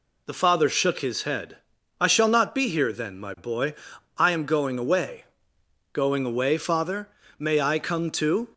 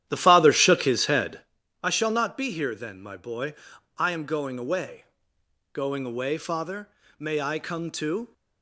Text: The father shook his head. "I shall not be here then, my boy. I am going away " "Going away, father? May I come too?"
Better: first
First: none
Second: starts louder than the rest; strong; until 1.5 s; 11.5 dB

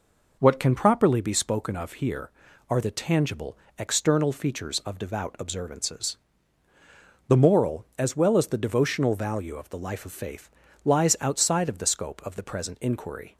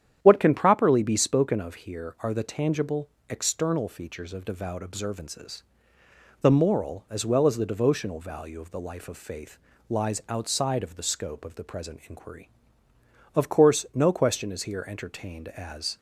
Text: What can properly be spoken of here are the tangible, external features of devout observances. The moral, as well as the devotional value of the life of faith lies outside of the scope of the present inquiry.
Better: first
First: pauses between "faith" and "lies"; at 10.4 s; 0.38 s long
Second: starts louder than the rest; strong; until 1.2 s; 9.5 dB // pauses between "faith" and "lies"; slight; at 9.5 s; 0.32 s long // goes on to say "Of course no question is here entertained as"; strong; from 13.3 s on; 2.6 s long

